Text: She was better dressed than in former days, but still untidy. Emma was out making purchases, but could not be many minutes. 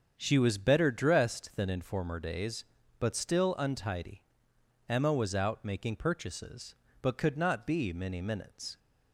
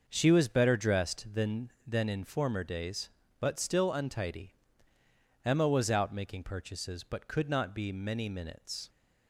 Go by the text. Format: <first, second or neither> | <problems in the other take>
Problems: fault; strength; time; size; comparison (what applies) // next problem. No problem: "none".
first | starts louder than the rest; until 1.0 s; 6 dB; strong in the first // says "than" twice; at 1.8 s